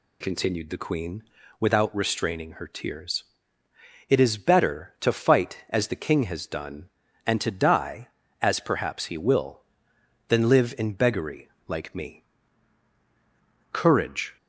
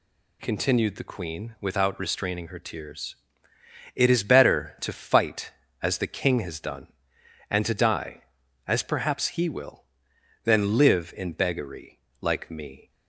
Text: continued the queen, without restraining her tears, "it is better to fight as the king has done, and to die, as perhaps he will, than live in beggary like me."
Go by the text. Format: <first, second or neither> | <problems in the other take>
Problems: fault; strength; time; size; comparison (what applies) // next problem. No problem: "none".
second | pauses between "beggary" and "like"; slight; at 11.4 s; 0.18 s long; slight in the second // goes on to say "Courage"; noticeable; from 13.7 s on; 0.64 s long